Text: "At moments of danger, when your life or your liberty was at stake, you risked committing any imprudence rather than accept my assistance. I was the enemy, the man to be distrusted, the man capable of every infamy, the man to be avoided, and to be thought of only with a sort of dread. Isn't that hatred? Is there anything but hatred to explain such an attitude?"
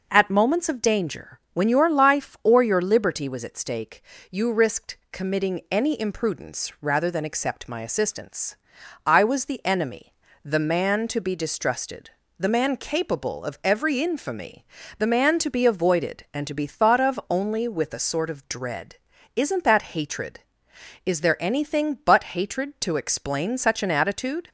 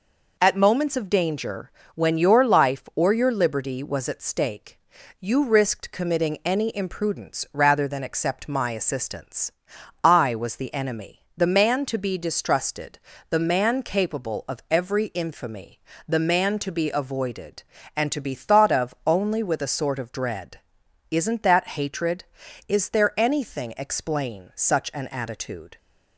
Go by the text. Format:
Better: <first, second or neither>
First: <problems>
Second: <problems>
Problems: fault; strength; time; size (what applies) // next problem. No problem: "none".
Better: first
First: none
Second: skips "but hatred to"; at 23.7 s